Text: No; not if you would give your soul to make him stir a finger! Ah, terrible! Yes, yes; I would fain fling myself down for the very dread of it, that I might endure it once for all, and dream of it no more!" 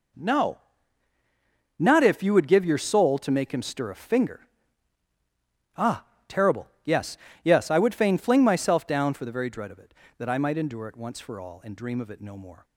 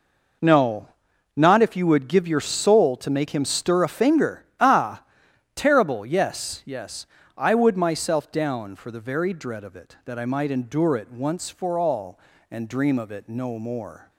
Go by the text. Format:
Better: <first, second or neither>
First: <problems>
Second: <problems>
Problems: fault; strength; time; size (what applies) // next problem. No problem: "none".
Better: first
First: none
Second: skips "fain fling"; at 7.7 s